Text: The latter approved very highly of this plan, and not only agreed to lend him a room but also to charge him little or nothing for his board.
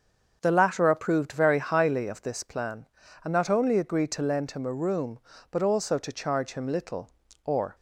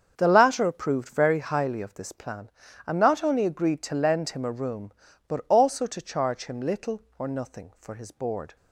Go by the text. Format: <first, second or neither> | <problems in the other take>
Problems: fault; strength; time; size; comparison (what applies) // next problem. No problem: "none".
second | starts louder than the rest; until 1.4 s; 6.5 dB; also in the second // stops before "nothing for his board"; at 7.7 s